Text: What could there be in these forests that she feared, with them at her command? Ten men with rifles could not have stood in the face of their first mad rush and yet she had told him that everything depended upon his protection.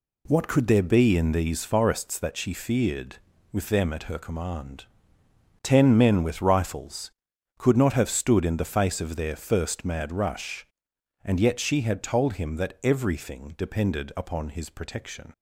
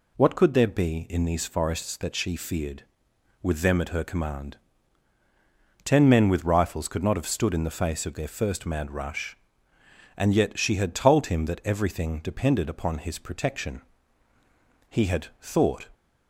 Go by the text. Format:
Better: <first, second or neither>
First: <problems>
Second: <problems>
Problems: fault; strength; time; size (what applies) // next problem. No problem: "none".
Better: first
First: none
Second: goes on to say "He had thought"; noticeable; from 14.8 s on; 1.0 s long